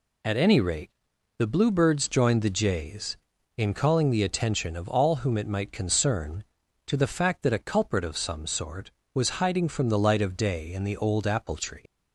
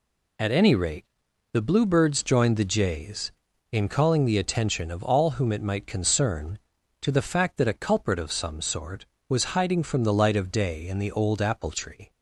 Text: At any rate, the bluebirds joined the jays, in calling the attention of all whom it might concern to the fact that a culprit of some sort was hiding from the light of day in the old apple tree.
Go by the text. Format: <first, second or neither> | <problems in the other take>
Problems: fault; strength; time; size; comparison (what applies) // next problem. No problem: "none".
second | leaves "tree" unfinished; at 11.8 s; 100 ms